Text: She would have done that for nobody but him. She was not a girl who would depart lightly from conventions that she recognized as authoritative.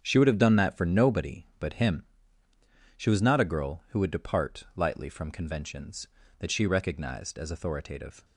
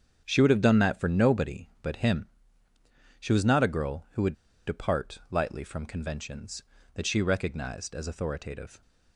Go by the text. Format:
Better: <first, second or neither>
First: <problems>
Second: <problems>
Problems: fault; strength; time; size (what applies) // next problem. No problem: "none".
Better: first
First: starts louder than the rest; strong; until 1.0 s; 7.5 dB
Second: starts louder than the rest; strong; until 1.2 s; 7.5 dB // pauses between "would" and "depart"; slight; at 4.3 s; 0.33 s long